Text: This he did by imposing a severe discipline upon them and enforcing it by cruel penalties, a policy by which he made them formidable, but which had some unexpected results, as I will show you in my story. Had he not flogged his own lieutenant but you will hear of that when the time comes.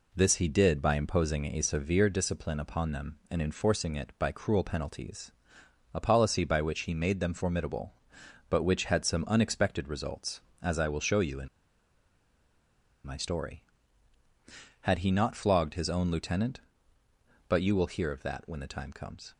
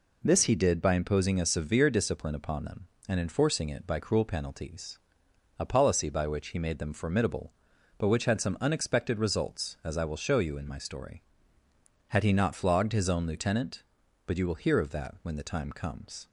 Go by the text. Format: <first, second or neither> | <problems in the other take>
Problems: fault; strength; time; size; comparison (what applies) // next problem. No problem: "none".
second | pauses between "in" and "my"; strong; at 11.4 s; 1.5 s long